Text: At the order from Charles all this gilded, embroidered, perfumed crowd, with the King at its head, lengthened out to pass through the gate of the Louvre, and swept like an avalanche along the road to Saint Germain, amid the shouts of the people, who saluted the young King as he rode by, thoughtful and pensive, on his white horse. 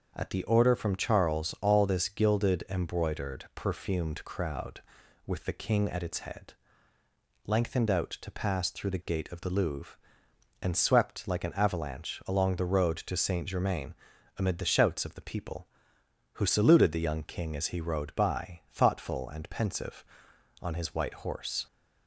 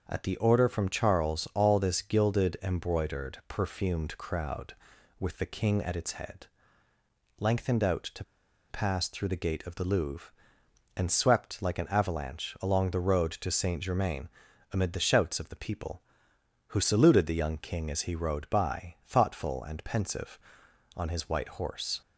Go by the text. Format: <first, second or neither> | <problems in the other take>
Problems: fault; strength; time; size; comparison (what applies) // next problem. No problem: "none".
first | starts louder than the rest; noticeable; until 1.0 s; 6 dB; noticeable in the first // pauses between "to" and "pass"; noticeable; at 8.2 s; 0.47 s long